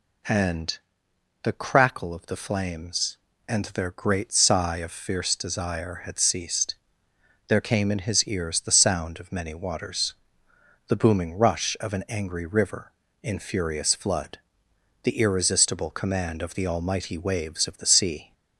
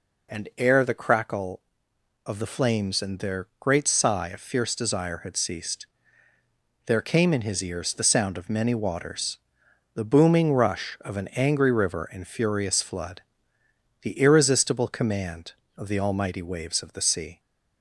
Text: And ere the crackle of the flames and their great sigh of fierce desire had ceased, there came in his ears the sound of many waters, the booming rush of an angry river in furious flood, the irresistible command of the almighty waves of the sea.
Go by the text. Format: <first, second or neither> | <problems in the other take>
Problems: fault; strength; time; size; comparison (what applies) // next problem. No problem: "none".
second | skips "ere"; at 1.0 s